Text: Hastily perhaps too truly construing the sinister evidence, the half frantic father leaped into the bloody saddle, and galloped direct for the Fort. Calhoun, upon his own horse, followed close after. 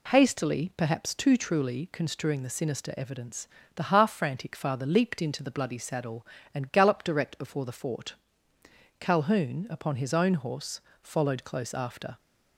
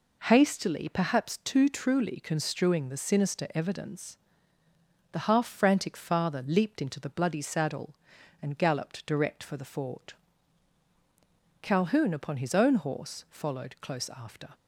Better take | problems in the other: second | says "before" for "for"; at 7.3 s

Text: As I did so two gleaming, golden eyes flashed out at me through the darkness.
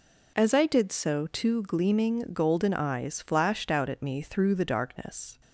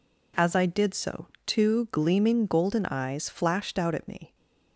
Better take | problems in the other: first | pauses between "so" and "two"; slight; at 1.2 s; 0.20 s long // stops before "through the darkness"; at 4.3 s

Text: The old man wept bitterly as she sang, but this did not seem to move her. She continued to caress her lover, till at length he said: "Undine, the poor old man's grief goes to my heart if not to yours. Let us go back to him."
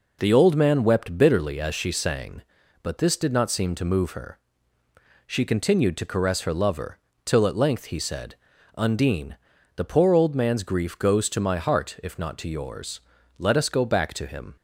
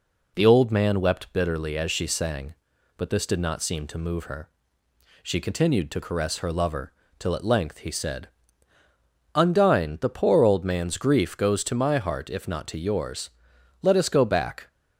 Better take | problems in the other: first | stops before "to him"; at 14.6 s

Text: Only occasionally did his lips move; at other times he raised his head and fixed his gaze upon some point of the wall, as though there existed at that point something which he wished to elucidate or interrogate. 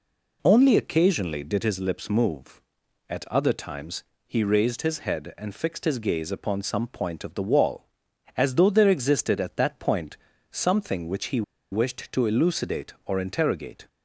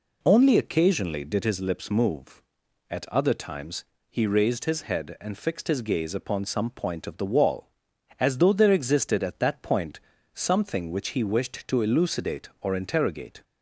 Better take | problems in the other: second | pauses between "times" and "he"; slight; at 4.0 s; 0.22 s long; slight in the second // pauses between "point" and "something"; slight; at 10.1 s; 0.34 s long; slight in the second // pauses between "he" and "wished"; slight; at 11.4 s; 0.29 s long

